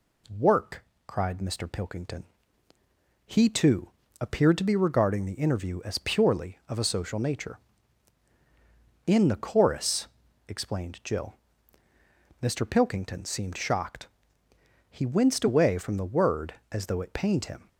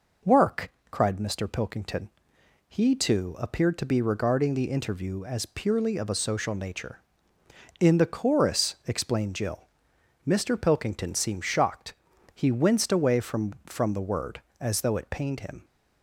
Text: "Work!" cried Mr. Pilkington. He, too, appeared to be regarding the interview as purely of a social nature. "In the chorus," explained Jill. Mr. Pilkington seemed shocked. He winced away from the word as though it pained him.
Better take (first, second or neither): first